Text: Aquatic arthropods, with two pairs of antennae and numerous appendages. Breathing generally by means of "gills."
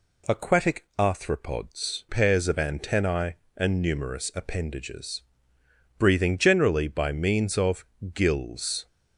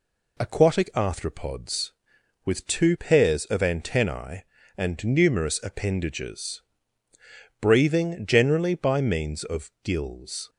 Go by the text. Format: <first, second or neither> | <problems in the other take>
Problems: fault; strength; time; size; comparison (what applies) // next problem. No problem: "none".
second | skips "with two"; at 2.0 s // pauses between "of" and "gills"; slight; at 7.8 s; 0.30 s long